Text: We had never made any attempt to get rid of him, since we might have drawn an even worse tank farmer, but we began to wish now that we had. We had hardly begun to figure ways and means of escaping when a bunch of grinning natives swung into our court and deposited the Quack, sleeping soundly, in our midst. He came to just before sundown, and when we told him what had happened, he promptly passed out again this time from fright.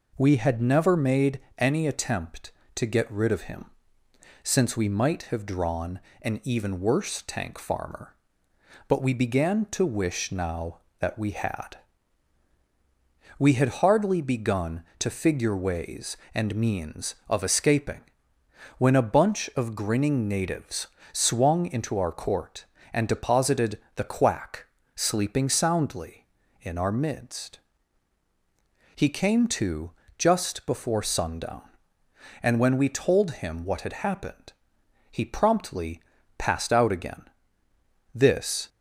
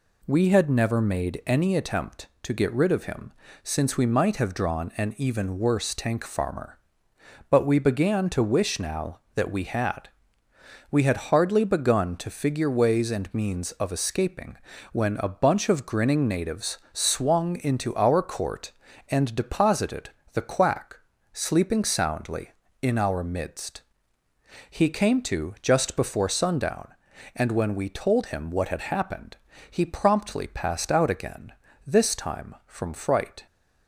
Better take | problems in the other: second | pauses between "made" and "any"; slight; at 1.4 s; 0.18 s long // pauses between "drawn" and "an"; slight; at 5.9 s; 0.24 s long // pauses between "escaping" and "when"; noticeable; at 18.0 s; 0.76 s long; slight in the second // pauses between "natives" and "swung"; slight; at 20.8 s; 0.26 s long // pauses between "deposited" and "the"; slight; at 23.7 s; 0.18 s long; slight in the second // pauses between "to" and "just"; slight; at 29.9 s; 0.26 s long // pauses between "promptly" and "passed"; at 36.0 s; 0.40 s long // pauses between "again" and "this"; noticeable; at 37.2 s; 0.90 s long; slight in the second // stops before "time from fright"; at 38.6 s

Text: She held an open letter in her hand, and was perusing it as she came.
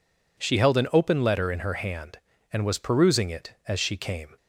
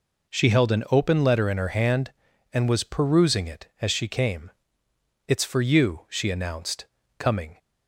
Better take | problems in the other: first | goes on to say "It's for you she announced coming"; strong; from 5.2 s on; 2.3 s long

